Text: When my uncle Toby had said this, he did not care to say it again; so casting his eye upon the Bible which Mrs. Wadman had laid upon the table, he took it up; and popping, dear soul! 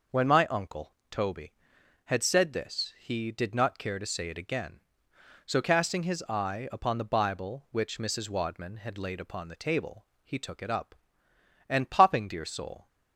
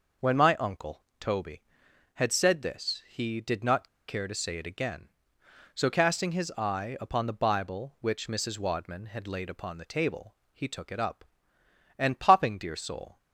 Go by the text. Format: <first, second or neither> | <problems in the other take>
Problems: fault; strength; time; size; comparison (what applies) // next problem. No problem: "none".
first | pauses between "uncle" and "Toby"; slight; at 1.0 s; 0.18 s long; slight in the first // pauses between "not" and "care"; slight; at 3.8 s; 0.19 s long